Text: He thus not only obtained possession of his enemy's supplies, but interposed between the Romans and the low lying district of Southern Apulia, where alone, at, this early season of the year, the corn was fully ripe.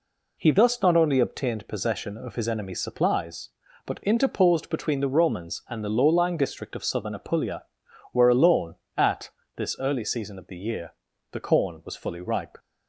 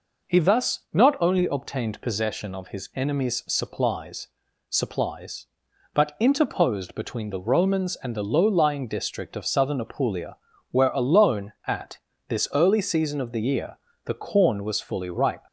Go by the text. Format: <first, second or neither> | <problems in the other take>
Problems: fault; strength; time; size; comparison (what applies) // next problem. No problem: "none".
first | says "supplies" twice; at 4.6 s